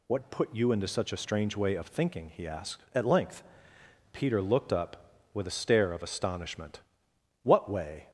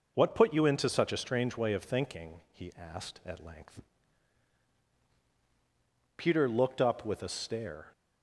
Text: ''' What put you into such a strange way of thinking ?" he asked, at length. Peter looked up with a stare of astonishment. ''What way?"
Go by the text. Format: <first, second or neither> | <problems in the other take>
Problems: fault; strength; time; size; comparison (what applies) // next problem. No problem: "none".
first | stops before "of astonishment What way"; at 7.9 s